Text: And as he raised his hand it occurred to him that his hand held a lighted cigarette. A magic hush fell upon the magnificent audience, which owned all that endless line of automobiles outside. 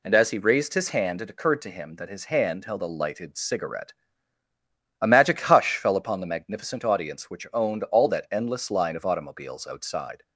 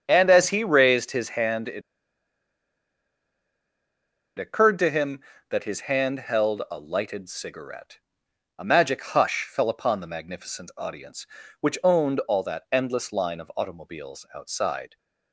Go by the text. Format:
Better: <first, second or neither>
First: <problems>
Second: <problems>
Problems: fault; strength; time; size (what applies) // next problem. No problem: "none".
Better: first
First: none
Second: starts louder than the rest; strong; until 1.0 s; 7.5 dB // pauses between "it" and "occurred"; strong; at 1.8 s; 2.5 s long